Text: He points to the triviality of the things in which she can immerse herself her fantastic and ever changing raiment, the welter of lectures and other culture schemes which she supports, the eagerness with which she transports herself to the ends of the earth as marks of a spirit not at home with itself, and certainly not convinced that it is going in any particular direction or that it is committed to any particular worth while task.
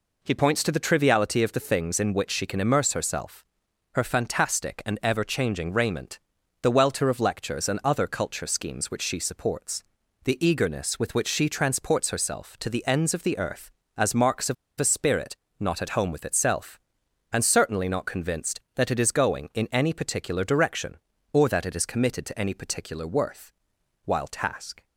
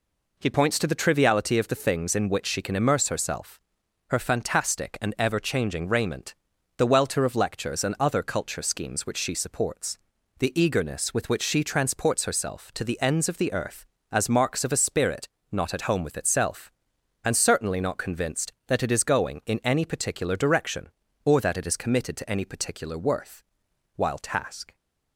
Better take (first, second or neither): second